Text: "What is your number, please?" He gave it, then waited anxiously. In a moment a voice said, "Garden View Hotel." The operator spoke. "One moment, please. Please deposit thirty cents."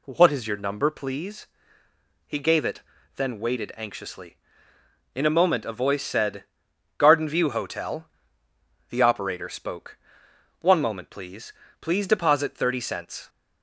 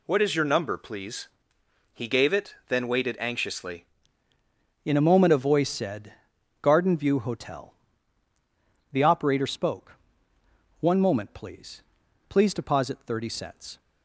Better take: first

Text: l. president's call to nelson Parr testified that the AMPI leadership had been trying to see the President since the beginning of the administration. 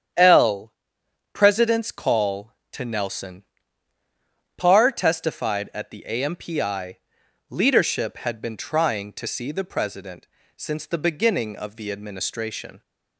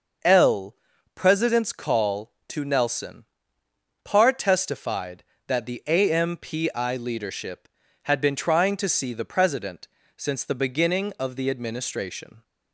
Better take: second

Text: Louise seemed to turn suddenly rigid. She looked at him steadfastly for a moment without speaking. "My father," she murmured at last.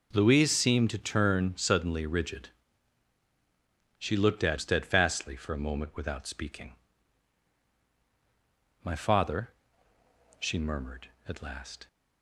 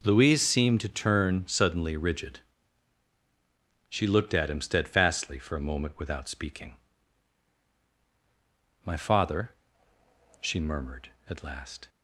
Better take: second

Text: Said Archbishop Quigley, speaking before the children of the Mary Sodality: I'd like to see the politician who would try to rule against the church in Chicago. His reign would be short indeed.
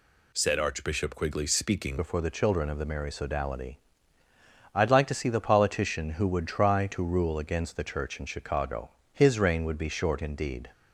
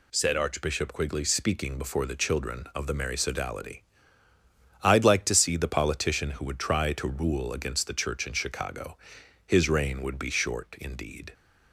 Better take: second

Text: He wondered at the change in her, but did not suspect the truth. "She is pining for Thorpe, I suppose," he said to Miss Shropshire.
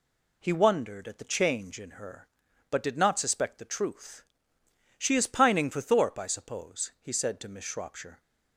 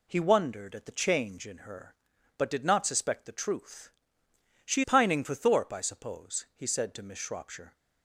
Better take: first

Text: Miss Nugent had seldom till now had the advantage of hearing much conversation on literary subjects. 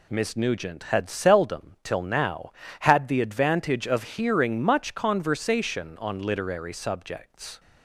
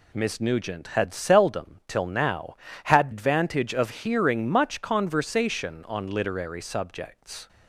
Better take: first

